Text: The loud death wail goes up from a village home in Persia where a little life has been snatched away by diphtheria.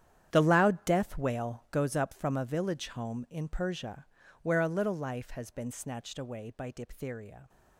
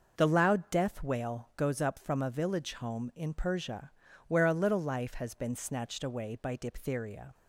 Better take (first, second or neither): second